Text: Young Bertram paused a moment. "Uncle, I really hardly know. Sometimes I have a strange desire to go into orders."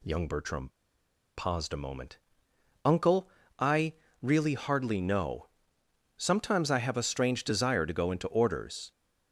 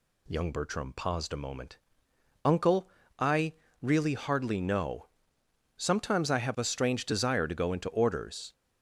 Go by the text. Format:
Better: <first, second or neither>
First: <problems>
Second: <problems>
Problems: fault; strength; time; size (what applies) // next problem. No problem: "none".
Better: second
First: pauses between "Bertram" and "paused"; noticeable; at 0.6 s; 0.67 s long // pauses between "I" and "really"; slight; at 3.9 s; 0.28 s long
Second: pauses between "I" and "really"; slight; at 3.5 s; 0.28 s long